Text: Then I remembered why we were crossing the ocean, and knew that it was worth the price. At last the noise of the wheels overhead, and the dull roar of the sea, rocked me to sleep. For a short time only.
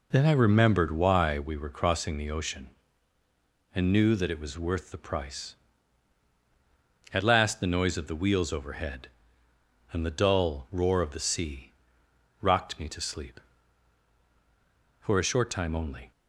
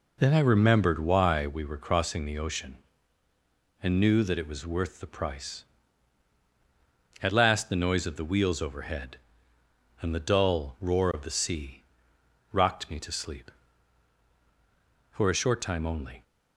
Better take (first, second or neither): neither